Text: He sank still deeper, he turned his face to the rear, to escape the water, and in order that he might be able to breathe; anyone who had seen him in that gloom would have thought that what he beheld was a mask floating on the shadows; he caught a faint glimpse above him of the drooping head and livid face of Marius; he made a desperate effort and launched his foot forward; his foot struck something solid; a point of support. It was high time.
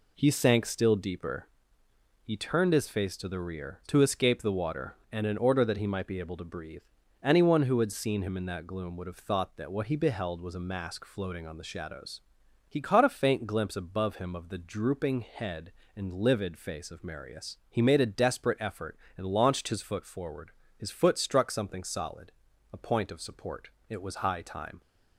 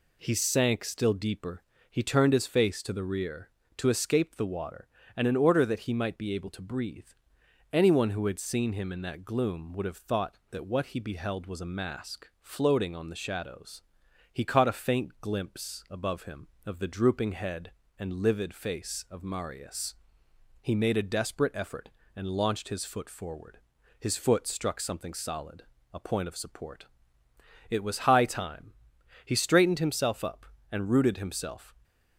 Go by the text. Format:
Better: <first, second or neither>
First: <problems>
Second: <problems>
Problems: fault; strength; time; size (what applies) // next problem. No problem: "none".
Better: first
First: none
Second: goes on to say "He straightened himself up and rooted himself"; strong; from 29.2 s on; 2.4 s long